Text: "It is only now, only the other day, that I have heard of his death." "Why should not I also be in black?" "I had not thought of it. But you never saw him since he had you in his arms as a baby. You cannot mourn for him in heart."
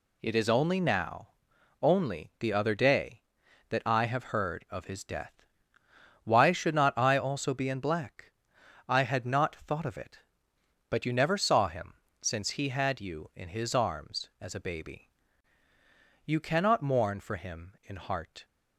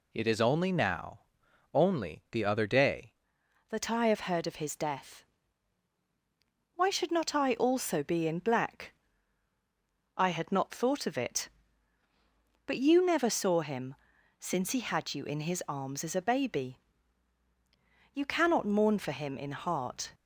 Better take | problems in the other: first | changes voice at "that"; from 3.6 s on; 16.5 s long // pauses between "him" and "since"; at 13.9 s; 0.42 s long; slight in the first

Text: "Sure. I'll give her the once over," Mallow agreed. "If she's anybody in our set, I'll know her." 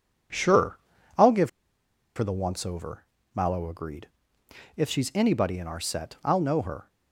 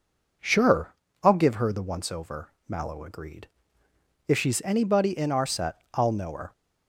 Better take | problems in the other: second | pauses between "give" and "her"; noticeable; at 1.4 s; 0.67 s long

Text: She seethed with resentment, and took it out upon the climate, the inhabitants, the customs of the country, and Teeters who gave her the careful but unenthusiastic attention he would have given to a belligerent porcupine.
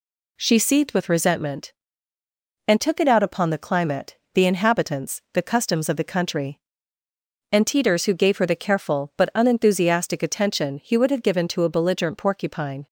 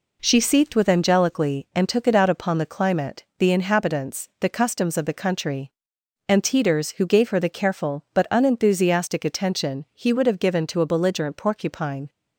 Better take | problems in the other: first | says "angelically" for "resentment"; at 0.8 s

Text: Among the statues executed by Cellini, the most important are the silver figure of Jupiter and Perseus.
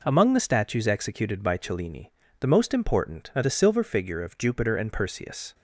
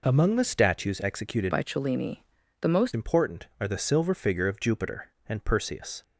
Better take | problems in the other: first | changes voice from "by" to "most"; from 1.5 to 2.9 s; 1.4 s long

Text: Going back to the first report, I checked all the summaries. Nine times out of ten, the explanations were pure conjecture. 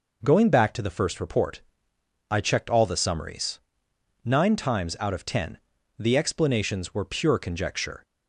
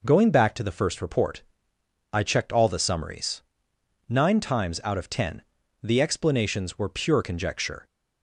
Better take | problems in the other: neither | none

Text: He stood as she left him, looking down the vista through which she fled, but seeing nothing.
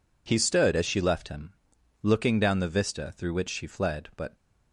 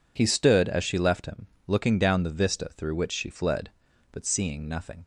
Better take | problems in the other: second | stops before "seeing nothing"; at 4.3 s

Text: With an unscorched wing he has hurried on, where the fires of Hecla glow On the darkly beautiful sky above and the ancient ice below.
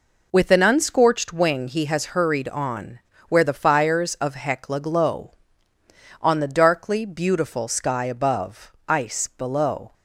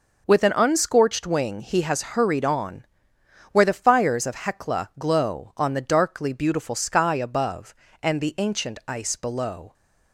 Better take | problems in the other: second | skips "and the ancient"; at 8.8 s

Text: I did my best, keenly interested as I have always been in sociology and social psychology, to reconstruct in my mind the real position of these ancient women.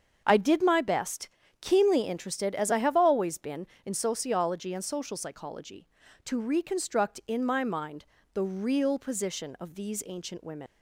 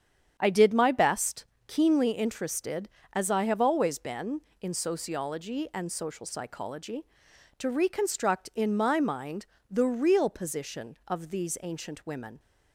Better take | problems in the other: second | starts louder than the rest; until 1.2 s; 7 dB; strong in the second // pauses between "mind" and "the"; slight; at 8.0 s; 0.28 s long; slight in the second // leaves "women" unfinished; at 10.6 s; 110 ms

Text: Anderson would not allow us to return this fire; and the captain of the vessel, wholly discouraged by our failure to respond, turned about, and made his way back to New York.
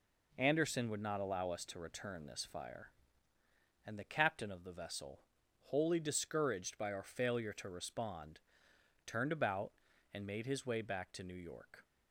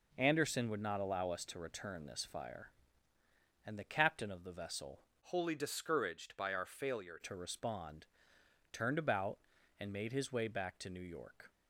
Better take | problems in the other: first | changes voice from "wholly" to "failure"; from 5.2 to 7.1 s; 1.9 s long

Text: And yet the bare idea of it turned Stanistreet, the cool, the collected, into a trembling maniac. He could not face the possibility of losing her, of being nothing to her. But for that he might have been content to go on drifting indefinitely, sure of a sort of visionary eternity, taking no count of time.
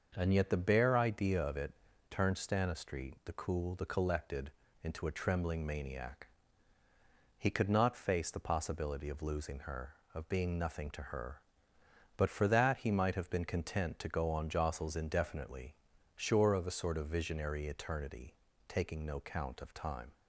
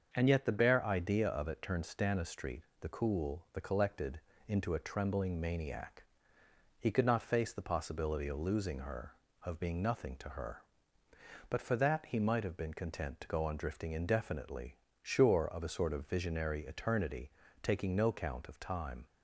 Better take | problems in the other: second | starts louder than the rest; until 1.1 s; 6 dB; also in the second // pauses between "it" and "turned"; slight; at 1.7 s; 0.36 s long // says "jostles" for "drifting"; at 14.4 s

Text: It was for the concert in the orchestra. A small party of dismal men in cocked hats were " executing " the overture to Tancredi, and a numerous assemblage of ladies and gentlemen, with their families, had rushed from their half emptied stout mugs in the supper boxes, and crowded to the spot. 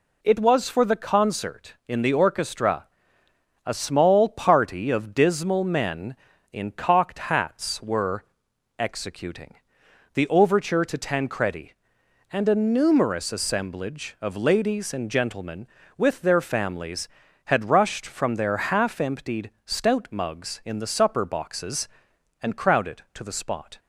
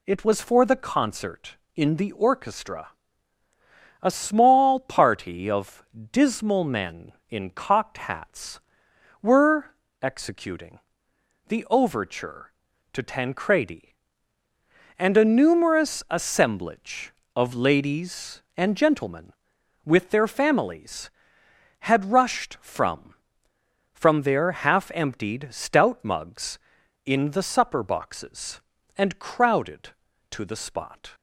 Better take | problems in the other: first | pauses between "of" and "dismal"; slight; at 5.8 s; 0.30 s long // says "from" twice; at 23.9 s

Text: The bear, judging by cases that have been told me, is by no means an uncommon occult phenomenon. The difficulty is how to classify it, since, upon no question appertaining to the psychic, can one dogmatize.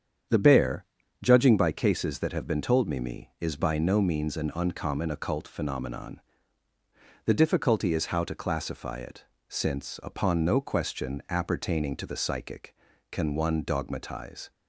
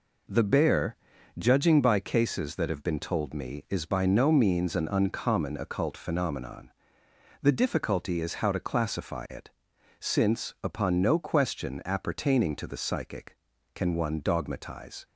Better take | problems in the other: second | starts louder than the rest; strong; until 1.6 s; 8 dB // says "me" twice; at 3.0 s

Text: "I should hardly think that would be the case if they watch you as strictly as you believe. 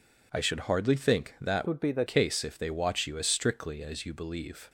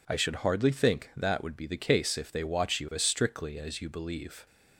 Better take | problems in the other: second | changes voice from "would" to "the"; from 1.6 to 2.0 s; 0.4 s long

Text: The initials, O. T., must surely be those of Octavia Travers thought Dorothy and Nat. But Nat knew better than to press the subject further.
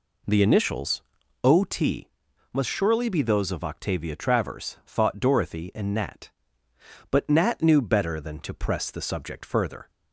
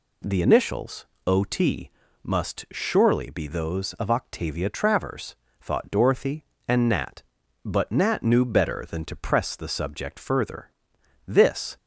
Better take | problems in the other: first | pauses between "Travers" and "thought"; slight; at 5.3 s; 0.26 s long // goes on to say "This"; from 11.2 s on; 0.50 s long

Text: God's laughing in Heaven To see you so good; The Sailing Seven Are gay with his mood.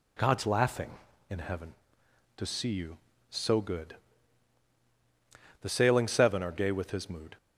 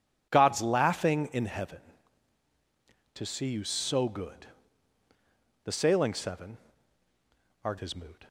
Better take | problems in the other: first | skips "gay with"; at 7.7 s

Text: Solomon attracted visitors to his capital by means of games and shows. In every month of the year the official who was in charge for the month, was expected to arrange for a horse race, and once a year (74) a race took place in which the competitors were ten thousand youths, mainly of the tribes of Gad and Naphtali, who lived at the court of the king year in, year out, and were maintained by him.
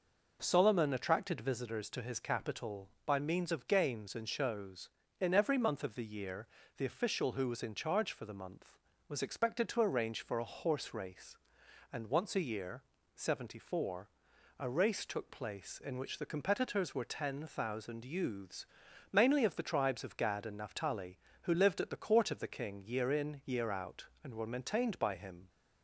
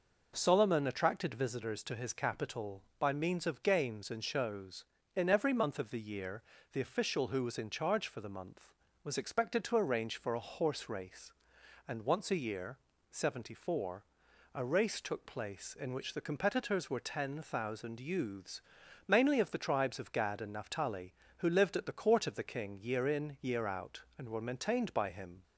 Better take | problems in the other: neither | pauses between "year" and "the"; slight; the same in both

